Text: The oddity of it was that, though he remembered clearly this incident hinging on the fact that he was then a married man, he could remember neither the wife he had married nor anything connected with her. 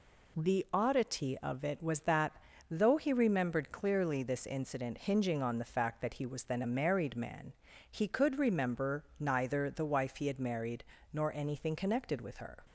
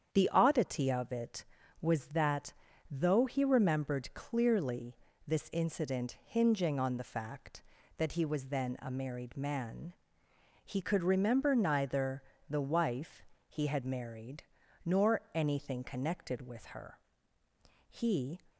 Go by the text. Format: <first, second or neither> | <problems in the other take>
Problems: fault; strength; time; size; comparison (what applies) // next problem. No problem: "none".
first | starts louder than the rest; strong; until 1.1 s; 8.5 dB // pauses between "clearly" and "this"; slight; at 4.9 s; 0.30 s long // pauses between "neither" and "the"; slight; at 12.2 s; 0.26 s long // pauses between "wife" and "he"; slight; at 13.2 s; 0.26 s long // pauses between "married" and "nor"; at 14.4 s; 0.42 s long; slight in the first // goes on to say "He"; from 17.8 s on; 0.52 s long